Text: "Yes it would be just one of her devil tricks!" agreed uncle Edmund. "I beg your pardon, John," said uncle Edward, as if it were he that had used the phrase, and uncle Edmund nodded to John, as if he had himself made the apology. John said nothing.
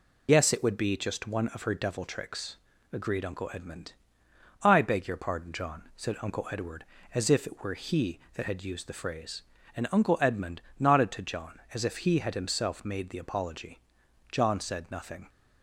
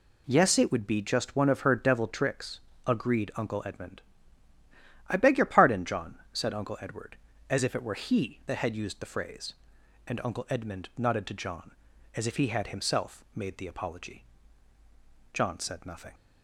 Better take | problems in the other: second | loses the start of "Yes"; at 0.2 s; 40 ms // pauses between "Edmund" and "nodded"; slight; at 10.6 s; 0.16 s long

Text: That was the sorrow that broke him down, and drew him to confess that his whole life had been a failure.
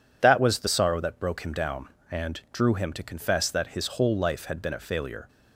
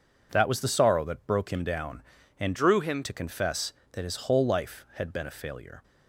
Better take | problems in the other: first | changes voice from "drew" to "him"; from 2.5 to 3.0 s; 0.5 s long

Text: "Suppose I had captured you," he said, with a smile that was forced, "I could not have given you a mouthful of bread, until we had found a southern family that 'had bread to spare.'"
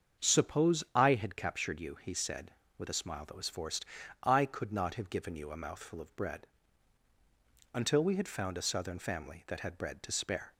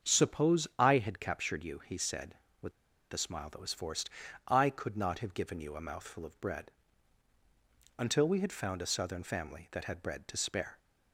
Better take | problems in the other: first | starts louder than the rest; strong; until 1.1 s; 7 dB; strong in the first // pauses between "with" and "a"; at 2.7 s; 0.40 s long

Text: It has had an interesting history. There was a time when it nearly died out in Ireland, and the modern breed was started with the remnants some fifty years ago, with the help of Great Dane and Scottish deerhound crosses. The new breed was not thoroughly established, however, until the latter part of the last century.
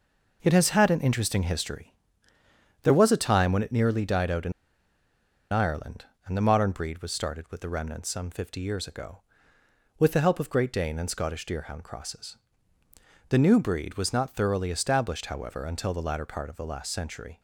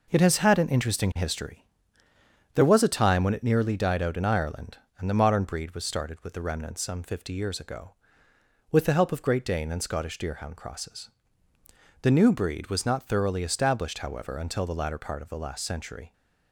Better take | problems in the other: second | pauses between "in" and "Ireland"; at 4.5 s; 1.0 s long

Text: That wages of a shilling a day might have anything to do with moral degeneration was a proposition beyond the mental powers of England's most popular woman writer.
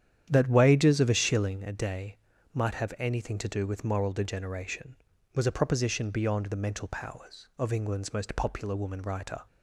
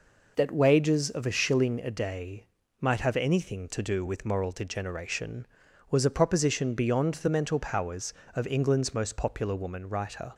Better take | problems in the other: second | starts louder than the rest; strong; until 1.6 s; 10 dB // pauses between "day" and "might"; slight; at 2.1 s; 0.36 s long; slight in the second

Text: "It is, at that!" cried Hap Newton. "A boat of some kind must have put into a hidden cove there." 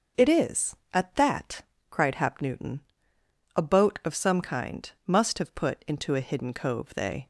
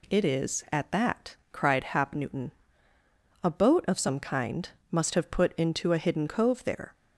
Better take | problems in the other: second | starts louder than the rest; noticeable; until 1.3 s; 6 dB // pauses between "kind" and "must"; slight; at 4.8 s; 0.16 s long; slight in the second // says "they" for "there"; at 6.9 s

